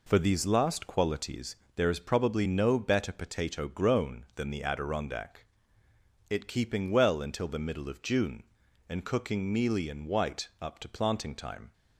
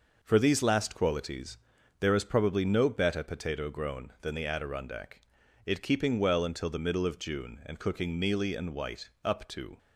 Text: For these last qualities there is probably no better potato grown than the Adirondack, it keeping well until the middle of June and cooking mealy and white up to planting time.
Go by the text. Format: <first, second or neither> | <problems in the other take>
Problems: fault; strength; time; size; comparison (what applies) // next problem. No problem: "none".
first | pauses between "qualities" and "there"; at 1.5 s; 0.42 s long; slight in the first // stops before "planting time"; at 9.7 s